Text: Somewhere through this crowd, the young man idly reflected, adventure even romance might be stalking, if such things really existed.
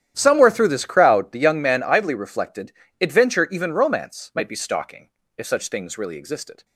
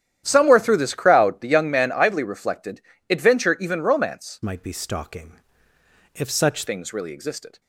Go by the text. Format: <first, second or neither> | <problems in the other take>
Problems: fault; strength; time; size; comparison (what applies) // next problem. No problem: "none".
first | starts louder than the rest; strong; until 1.2 s; 11 dB; strong in the first // changes voice from "might" to "such"; from 4.4 to 6.6 s; 2.2 s long